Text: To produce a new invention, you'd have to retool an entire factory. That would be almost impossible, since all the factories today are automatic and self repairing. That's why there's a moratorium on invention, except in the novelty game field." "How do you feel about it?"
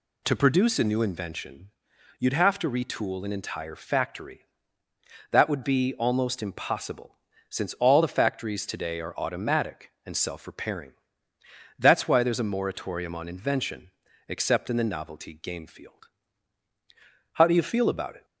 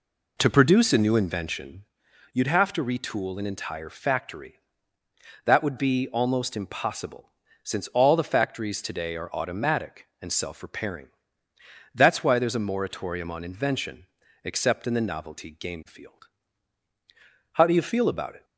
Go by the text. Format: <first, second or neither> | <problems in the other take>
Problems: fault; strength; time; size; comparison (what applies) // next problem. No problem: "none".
first | starts louder than the rest; slight; until 1.9 s; 3 dB